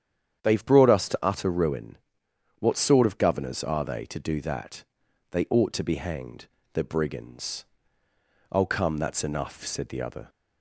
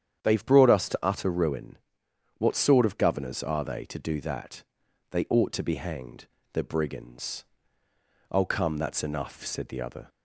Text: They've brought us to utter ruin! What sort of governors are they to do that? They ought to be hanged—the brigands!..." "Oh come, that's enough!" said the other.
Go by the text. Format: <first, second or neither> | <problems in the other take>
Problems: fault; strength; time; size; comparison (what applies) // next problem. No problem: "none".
neither | starts louder than the rest; strong; the same in both